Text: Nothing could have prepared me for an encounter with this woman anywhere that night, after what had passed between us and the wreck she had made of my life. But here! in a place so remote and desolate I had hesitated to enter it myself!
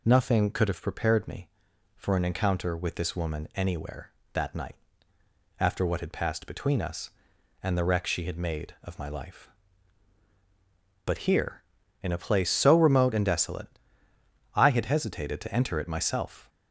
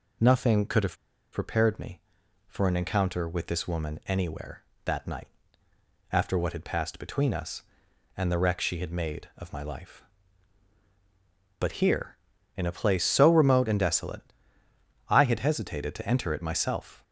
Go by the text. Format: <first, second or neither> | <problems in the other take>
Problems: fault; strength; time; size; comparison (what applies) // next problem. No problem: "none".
first | pauses between "have" and "prepared"; at 0.9 s; 0.36 s long // pauses between "desolate" and "I"; noticeable; at 14.2 s; 0.88 s long; noticeable in the first